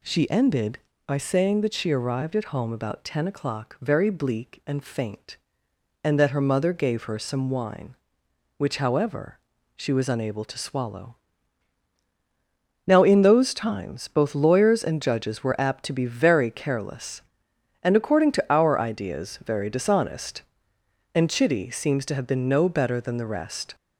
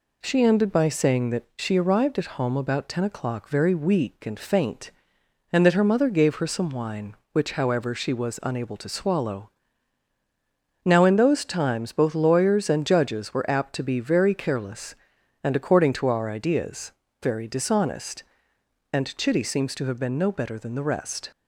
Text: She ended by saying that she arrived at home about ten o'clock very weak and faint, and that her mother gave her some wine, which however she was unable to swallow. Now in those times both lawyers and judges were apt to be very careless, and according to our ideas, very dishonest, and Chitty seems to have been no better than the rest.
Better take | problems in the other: second | says "bleak" for "weak"; at 4.0 s // pauses between "however" and "she"; at 9.3 s; 0.38 s long

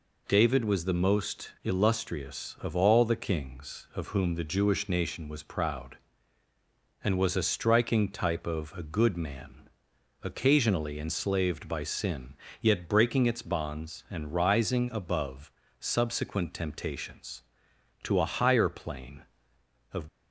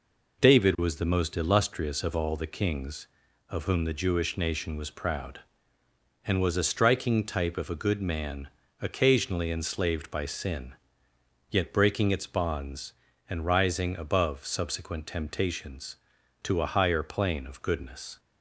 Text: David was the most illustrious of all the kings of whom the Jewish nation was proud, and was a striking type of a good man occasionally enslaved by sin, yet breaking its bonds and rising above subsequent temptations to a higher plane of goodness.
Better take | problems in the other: second | pauses between "man" and "occasionally"; noticeable; at 9.6 s; 0.62 s long; slight in the second // pauses between "above" and "subsequent"; slight; at 15.5 s; 0.28 s long // stops before "goodness"; at 20.0 s

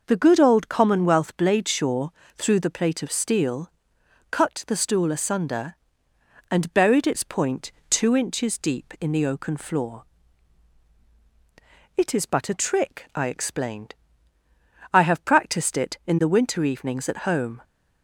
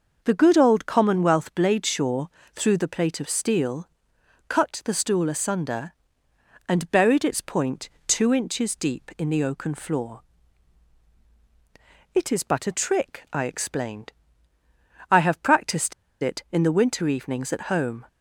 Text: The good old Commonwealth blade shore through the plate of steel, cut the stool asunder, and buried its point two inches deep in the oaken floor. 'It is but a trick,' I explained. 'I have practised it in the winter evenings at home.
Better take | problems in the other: first | pauses between "shore" and "through"; slight; at 2.2 s; 0.26 s long; slight in the first // pauses between "point" and "two"; slight; at 7.8 s; 0.16 s long; slight in the first // pauses between "practised" and "it"; slight; at 15.9 s; 0.29 s long

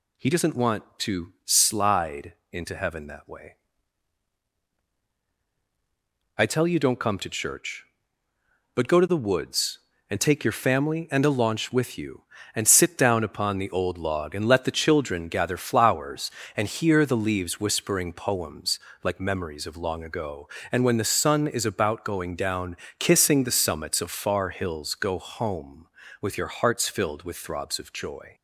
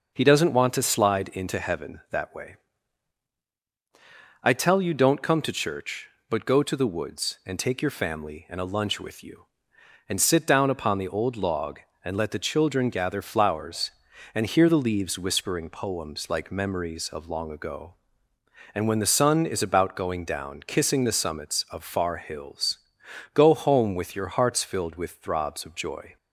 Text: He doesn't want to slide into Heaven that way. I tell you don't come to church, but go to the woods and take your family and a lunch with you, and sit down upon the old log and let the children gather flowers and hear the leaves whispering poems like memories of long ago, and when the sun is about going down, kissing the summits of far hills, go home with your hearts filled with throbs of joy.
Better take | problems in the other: second | pauses between "slide" and "into"; slight; at 2.3 s; 0.18 s long // says "launch" for "lunch"; at 11.3 s // pauses between "poems" and "like"; slight; at 18.7 s; 0.24 s long

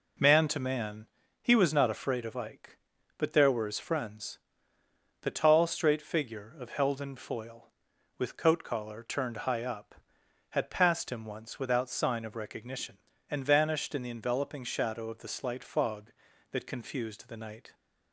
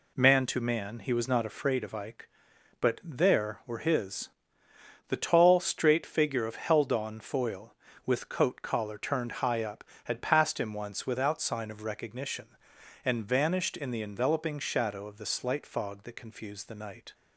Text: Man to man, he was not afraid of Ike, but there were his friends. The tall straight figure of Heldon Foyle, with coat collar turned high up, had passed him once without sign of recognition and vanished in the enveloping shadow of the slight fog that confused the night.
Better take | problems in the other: first | skips "friends"; at 4.6 s

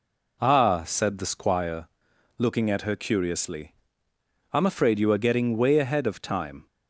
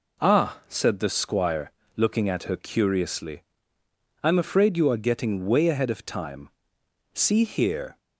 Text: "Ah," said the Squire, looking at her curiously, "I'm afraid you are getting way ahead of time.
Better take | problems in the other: first | goes on to say "See here"; noticeable; from 7.1 s on; 0.84 s long

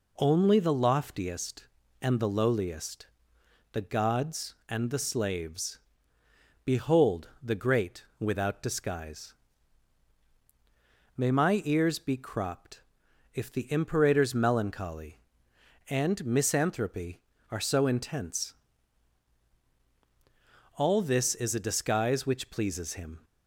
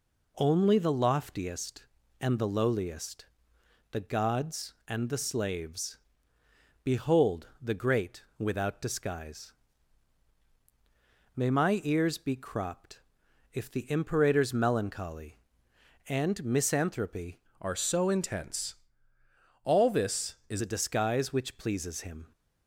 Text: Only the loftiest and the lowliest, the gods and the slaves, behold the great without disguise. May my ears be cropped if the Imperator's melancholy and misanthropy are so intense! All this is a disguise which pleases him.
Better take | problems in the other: first | pauses between "behold" and "the"; slight; at 7.4 s; 0.16 s long; slight in the first // pauses between "cropped" and "if"; noticeable; at 12.9 s; 0.54 s long; noticeable in the first // changes voice from "are" to "is"; from 17.6 to 20.6 s; 3.0 s long

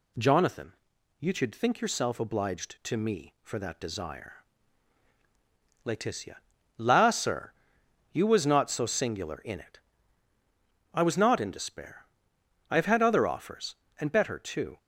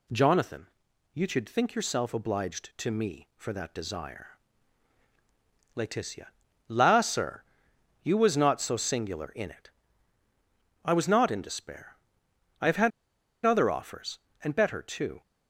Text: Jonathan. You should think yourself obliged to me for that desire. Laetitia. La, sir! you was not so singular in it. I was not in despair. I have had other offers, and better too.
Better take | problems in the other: first | pauses between "had" and "other"; noticeable; at 12.9 s; 0.53 s long

